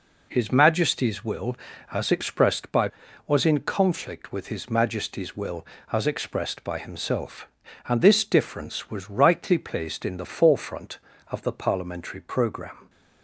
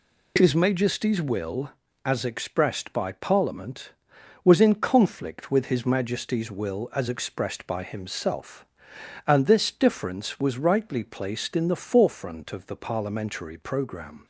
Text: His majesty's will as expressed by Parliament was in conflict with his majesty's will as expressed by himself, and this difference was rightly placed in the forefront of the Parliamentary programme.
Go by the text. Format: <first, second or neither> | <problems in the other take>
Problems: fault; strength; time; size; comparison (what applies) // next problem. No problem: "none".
second | skips "Parliament"; at 3.0 s